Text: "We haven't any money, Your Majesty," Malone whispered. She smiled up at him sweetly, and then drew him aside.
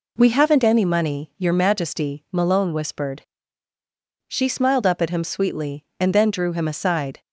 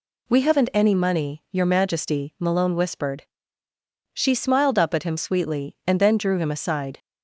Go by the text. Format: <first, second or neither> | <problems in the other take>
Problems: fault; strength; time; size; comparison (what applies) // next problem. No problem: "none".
neither | none